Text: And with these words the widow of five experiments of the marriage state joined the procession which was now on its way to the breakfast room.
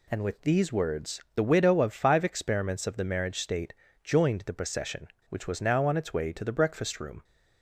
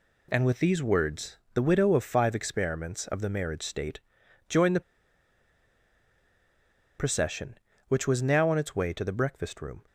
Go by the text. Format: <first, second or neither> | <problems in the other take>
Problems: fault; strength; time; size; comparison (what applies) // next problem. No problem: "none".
first | pauses between "words" and "the"; slight; at 1.3 s; 0.18 s long // pauses between "state" and "joined"; noticeable; at 3.9 s; 0.48 s long; slight in the first // pauses between "the" and "procession"; strong; at 4.8 s; 2.1 s long